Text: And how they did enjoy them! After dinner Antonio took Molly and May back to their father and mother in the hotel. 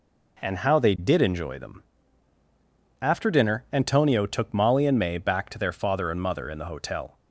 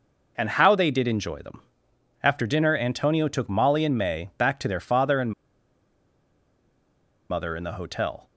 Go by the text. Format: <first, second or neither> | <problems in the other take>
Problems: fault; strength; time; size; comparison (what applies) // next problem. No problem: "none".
first | pauses between "and" and "mother"; strong; at 5.3 s; 1.9 s long